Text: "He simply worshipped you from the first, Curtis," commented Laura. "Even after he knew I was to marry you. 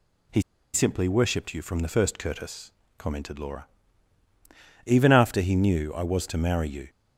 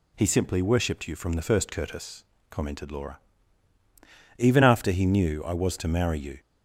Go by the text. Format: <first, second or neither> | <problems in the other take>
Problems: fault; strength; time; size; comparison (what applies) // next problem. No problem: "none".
second | pauses between "He" and "simply"; slight; at 0.4 s; 0.33 s long